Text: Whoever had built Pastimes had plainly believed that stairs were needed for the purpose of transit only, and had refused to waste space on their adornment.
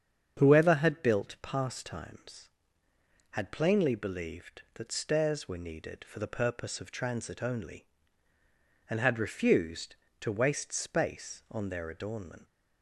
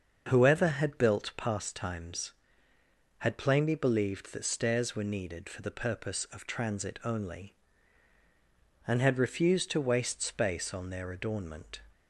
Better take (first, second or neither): neither